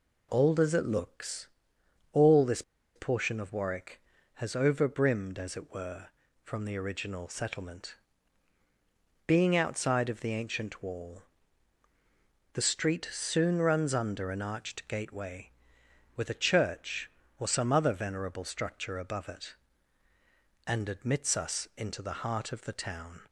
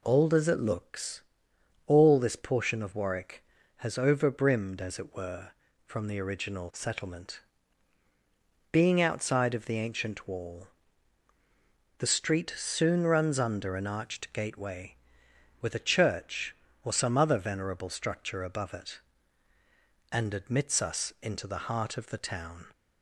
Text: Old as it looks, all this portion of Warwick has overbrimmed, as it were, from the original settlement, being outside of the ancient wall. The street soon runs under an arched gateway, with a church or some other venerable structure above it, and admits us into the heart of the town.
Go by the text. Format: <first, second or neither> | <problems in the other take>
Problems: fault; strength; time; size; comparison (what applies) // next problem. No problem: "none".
second | pauses between "this" and "portion"; slight; at 2.6 s; 0.33 s long